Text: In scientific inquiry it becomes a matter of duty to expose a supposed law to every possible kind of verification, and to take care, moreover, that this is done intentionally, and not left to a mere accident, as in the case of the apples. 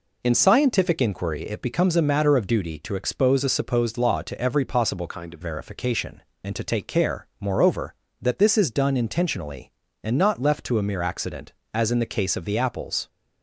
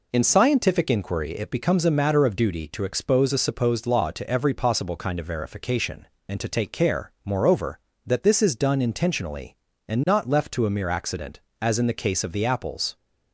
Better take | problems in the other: second | changes voice from "kind" to "of"; from 5.0 to 5.4 s; 0.4 s long

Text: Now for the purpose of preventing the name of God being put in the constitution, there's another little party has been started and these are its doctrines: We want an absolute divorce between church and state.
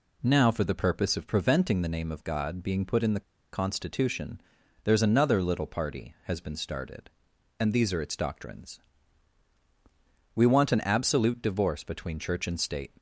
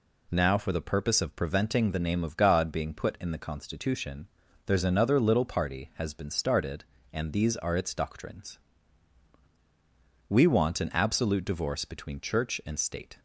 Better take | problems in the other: second | pauses between "the" and "constitution"; slight; at 3.2 s; 0.32 s long

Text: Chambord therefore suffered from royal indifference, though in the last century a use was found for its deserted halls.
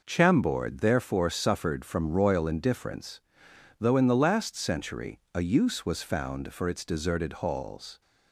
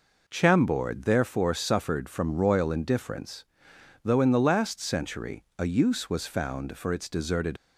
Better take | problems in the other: first | stops before "halls"; at 7.5 s

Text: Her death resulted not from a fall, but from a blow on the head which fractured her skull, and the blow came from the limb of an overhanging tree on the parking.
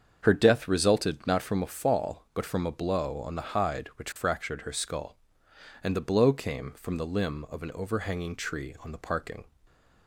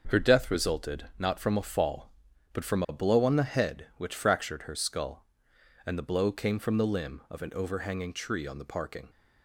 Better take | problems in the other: second | starts louder than the rest; until 1.2 s; 7 dB; also in the second // says "hide" for "head"; at 3.5 s // stays silent after the last word; slight; from 9.4 s on; 0.6 s long

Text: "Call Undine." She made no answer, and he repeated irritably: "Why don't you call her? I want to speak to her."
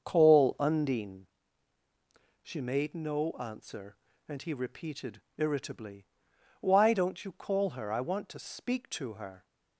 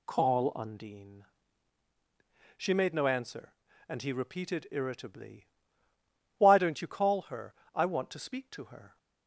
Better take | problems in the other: second | starts louder than the rest; until 1.1 s; 6.5 dB // pauses between "repeated" and "irritably"; slight; at 5.2 s; 0.16 s long

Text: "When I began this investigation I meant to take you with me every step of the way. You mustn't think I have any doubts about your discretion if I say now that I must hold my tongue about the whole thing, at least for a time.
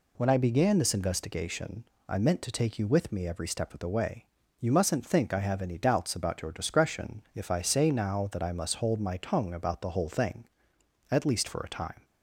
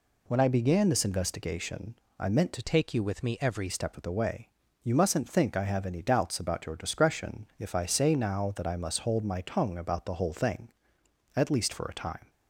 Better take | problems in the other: first | pauses between "investigation" and "I"; slight; at 1.9 s; 0.24 s long; slight in the first // changes voice from "take" to "every"; from 2.6 to 3.6 s; 1.0 s long

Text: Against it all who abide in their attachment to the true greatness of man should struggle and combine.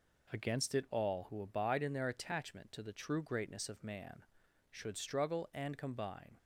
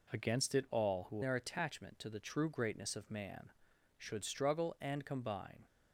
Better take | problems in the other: first | skips "abide in"; at 1.2 s

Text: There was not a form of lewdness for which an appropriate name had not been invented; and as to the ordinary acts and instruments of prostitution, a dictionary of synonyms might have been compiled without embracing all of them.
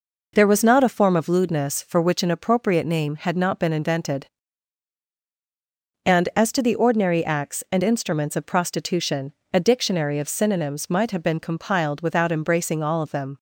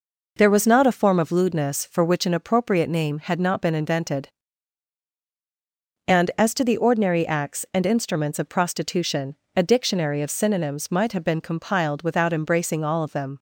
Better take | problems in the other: neither | none

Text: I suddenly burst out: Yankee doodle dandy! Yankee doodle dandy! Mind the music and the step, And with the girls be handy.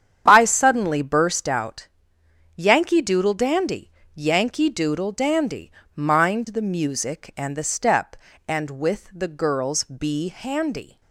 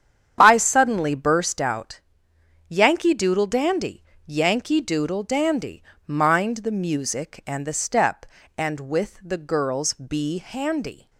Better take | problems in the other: neither | starts louder than the rest; strong; the same in both

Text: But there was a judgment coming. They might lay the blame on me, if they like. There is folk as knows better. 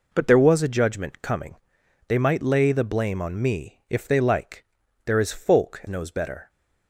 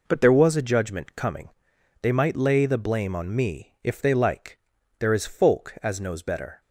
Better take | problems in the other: second | skips "as"; at 5.8 s

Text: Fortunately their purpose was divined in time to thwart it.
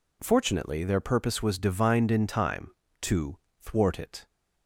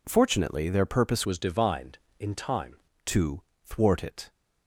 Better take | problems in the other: first | changes voice from "was" to "time"; from 1.2 to 2.7 s; 1.5 s long // pauses between "to" and "thwart"; slight; at 3.4 s; 0.26 s long; slight in the first

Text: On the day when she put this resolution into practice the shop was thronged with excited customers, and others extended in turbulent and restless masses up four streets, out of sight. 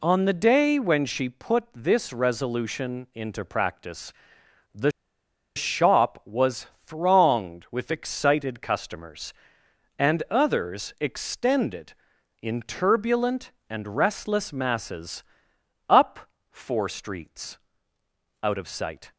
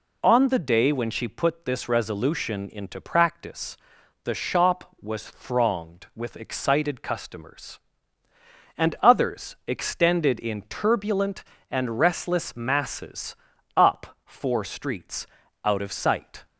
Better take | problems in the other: second | pauses between "practice" and "the"; noticeable; at 4.1 s; 0.60 s long; noticeable in the second // pauses between "the" and "shop"; noticeable; at 4.9 s; 0.65 s long // pauses between "was" and "thronged"; slight; at 6.6 s; 0.20 s long // pauses between "masses" and "up"; noticeable; at 15.2 s; 0.64 s long; also in the second // pauses between "up" and "four"; slight; at 16.2 s; 0.22 s long

